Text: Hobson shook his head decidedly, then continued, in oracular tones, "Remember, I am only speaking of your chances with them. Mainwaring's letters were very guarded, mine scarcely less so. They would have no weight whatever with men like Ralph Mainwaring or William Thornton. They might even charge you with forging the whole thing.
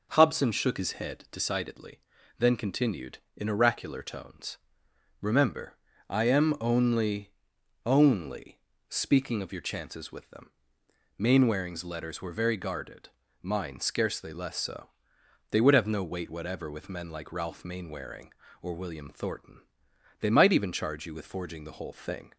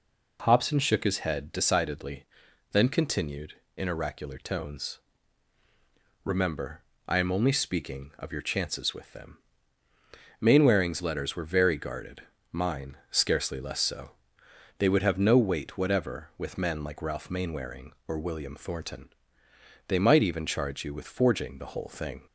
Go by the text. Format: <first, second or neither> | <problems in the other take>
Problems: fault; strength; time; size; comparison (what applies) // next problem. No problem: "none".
second | says "only" twice; at 7.8 s